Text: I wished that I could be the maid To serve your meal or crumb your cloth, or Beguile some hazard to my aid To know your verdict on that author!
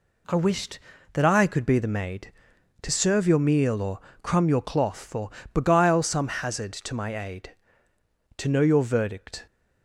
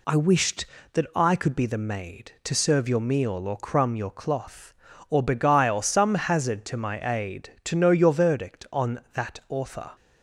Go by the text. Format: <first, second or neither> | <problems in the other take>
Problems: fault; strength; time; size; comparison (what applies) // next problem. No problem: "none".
second | pauses between "or" and "crumb"; slight; at 3.9 s; 0.24 s long // pauses between "or" and "Beguile"; slight; at 5.2 s; 0.24 s long // stops before "on that author"; at 9.4 s